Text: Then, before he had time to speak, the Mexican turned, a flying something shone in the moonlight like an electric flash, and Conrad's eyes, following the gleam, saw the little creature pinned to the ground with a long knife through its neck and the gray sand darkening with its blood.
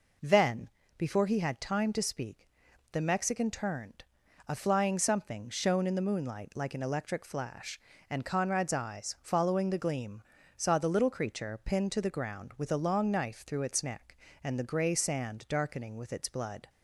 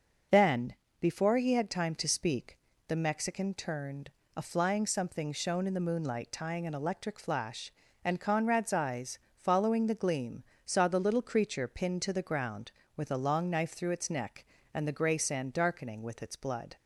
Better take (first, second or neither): first